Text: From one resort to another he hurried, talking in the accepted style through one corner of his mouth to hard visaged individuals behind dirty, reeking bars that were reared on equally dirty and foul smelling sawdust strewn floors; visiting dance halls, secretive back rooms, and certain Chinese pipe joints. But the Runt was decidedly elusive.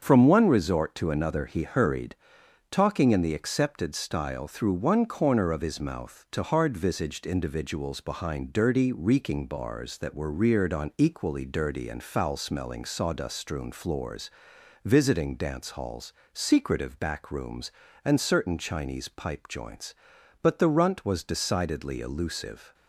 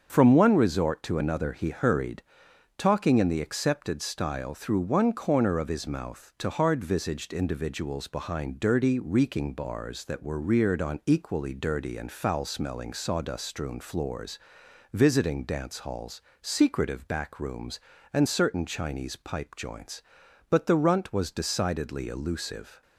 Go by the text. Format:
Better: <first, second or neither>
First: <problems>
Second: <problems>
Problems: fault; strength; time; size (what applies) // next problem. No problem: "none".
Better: neither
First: starts louder than the rest; until 1.0 s; 7 dB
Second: starts louder than the rest; until 1.1 s; 7 dB